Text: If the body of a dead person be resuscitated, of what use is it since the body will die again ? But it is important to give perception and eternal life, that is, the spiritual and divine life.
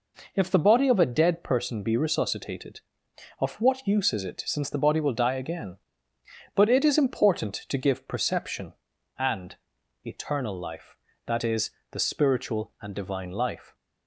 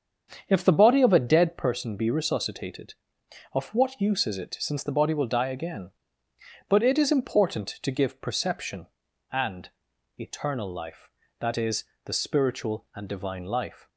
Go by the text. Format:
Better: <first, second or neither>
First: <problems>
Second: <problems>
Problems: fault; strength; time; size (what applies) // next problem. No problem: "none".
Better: first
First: pauses between "and" and "eternal"; noticeable; at 9.5 s; 0.48 s long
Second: starts louder than the rest; strong; until 1.6 s; 7.5 dB // pauses between "and" and "eternal"; noticeable; at 9.7 s; 0.48 s long